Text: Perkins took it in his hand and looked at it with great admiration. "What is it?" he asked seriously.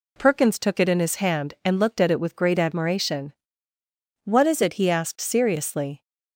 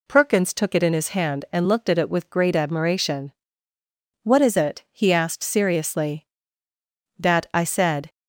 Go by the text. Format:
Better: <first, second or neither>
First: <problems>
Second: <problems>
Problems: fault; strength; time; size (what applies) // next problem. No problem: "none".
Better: first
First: none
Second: goes on to say "That I said"; noticeable; from 7.1 s on; 0.94 s long